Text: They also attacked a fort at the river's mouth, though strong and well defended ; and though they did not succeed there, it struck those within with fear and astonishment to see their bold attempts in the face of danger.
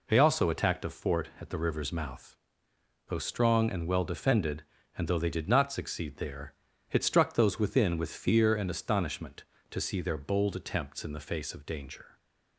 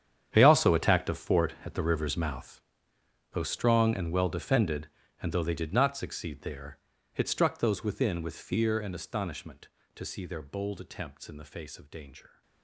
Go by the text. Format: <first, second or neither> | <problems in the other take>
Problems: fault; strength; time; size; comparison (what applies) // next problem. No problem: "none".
first | gets quieter; strong; throughout; 16.5 dB